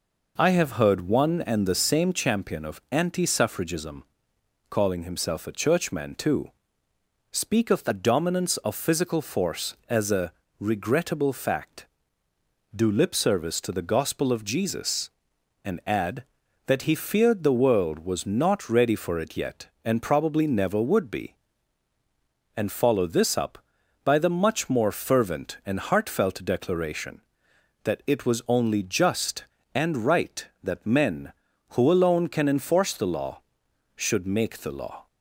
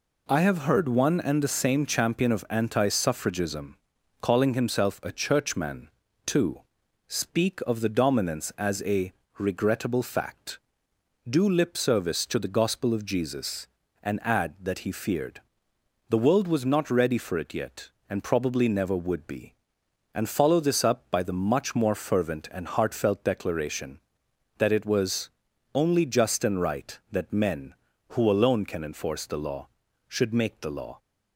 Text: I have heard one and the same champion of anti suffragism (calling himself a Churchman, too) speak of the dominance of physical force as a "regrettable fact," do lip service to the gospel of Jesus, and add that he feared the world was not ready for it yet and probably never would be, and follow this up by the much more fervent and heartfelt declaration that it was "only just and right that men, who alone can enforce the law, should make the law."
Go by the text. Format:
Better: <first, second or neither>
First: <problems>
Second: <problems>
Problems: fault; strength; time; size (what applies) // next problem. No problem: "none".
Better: first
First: pauses between "a" and "regrettable"; slight; at 10.3 s; 0.28 s long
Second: skips "of physical force"; at 8.5 s // pauses between "a" and "regrettable"; slight; at 9.1 s; 0.26 s long // pauses between "feared" and "the"; noticeable; at 15.4 s; 0.66 s long // pauses between "was" and "only"; at 25.3 s; 0.42 s long